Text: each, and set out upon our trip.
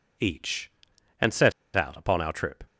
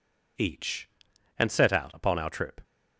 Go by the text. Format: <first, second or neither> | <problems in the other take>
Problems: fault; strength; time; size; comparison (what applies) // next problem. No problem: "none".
second | pauses between "set" and "out"; slight; at 1.5 s; 0.23 s long